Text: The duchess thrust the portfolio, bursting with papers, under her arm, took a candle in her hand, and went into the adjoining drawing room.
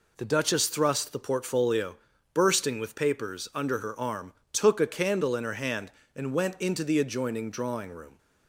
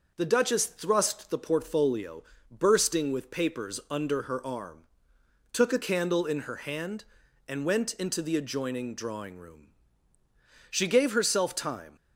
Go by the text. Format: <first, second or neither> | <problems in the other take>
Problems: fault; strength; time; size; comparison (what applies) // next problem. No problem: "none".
first | goes on to say "She gave herself time"; noticeable; from 10.6 s on; 1.2 s long